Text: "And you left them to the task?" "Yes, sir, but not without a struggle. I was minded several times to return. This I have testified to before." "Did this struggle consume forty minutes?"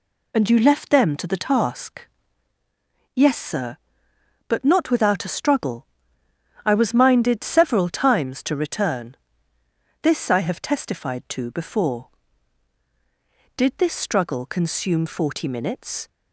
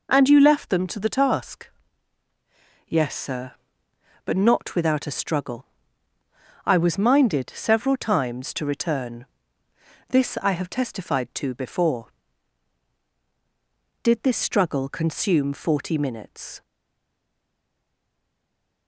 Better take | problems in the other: first | stays silent after the last word; from 16.6 s on; 2.2 s long

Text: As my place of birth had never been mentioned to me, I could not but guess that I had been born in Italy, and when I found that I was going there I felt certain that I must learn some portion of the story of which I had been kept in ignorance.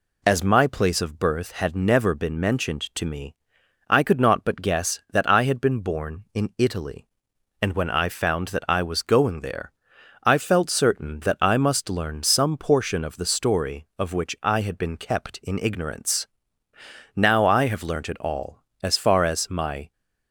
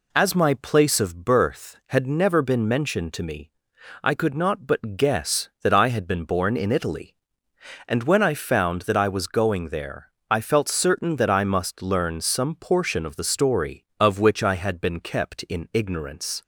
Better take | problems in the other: second | pauses between "there" and "I"; noticeable; at 9.7 s; 0.50 s long; slight in the second // goes on to say "Now I have learnt it all as far as my"; strong; from 17.1 s on; 2.7 s long

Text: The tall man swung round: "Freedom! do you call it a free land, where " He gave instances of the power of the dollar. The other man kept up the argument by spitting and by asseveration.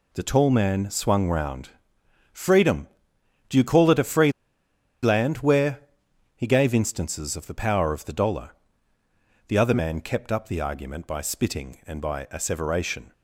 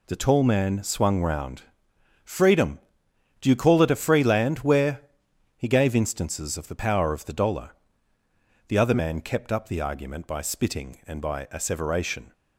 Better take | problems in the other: second | pauses between "free" and "land"; noticeable; at 4.3 s; 0.71 s long

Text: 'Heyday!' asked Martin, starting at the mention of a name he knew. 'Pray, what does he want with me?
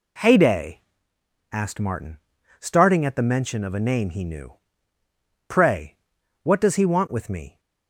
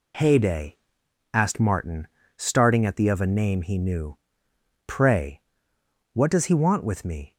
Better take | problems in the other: first | skips "mention"; at 3.0 s

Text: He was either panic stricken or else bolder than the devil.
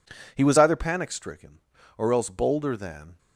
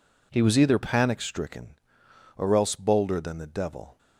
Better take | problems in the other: second | stops before "the devil"; at 3.1 s

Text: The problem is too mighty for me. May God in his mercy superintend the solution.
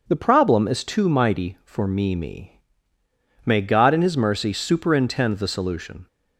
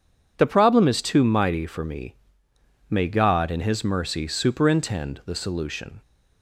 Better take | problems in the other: second | starts louder than the rest; noticeable; until 1.0 s; 6 dB // says "me" twice; at 2.1 s

